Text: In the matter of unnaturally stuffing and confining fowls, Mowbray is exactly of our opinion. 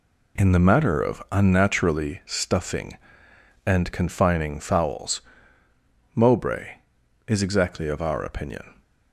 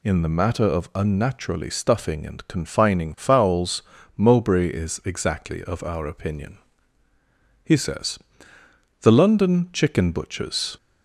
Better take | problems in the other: first | goes on to say "He says The London chicken butchers"; strong; from 7.6 s on; 3.1 s long

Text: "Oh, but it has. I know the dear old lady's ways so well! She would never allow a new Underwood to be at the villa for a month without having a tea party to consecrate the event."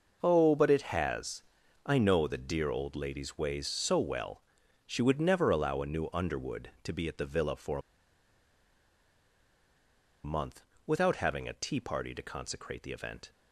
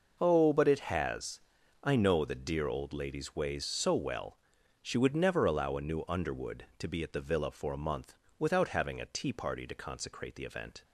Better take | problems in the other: second | pauses between "for" and "a"; strong; at 7.7 s; 2.4 s long // pauses between "month" and "without"; slight; at 10.6 s; 0.24 s long; slight in the second

